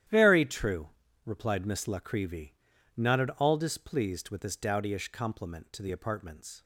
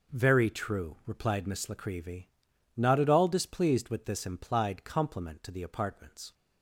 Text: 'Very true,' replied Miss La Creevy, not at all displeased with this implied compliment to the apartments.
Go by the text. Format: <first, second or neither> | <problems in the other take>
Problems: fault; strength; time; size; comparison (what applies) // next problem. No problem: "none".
second | starts louder than the rest; strong; until 1.4 s; 11.5 dB // says "dowdyish" for "implied"; at 4.5 s